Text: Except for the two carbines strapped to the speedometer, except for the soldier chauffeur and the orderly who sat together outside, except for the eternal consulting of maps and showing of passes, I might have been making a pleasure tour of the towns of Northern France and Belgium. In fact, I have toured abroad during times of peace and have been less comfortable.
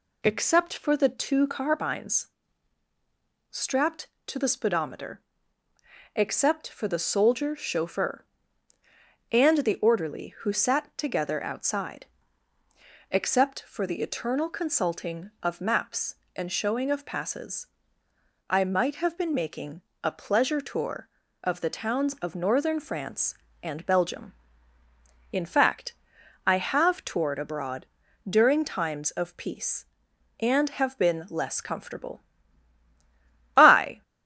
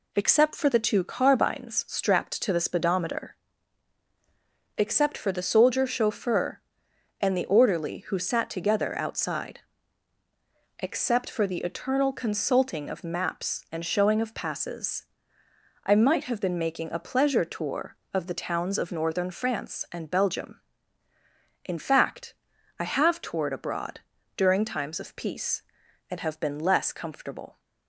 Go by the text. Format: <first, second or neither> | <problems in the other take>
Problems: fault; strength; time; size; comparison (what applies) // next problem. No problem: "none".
second | pauses between "carbines" and "strapped"; at 2.2 s; 1.2 s long // pauses between "making" and "a"; slight; at 19.8 s; 0.20 s long // pauses between "abroad" and "during"; at 27.8 s; 0.42 s long; slight in the second // goes on to say "I"; slight; from 33.5 s on; 0.46 s long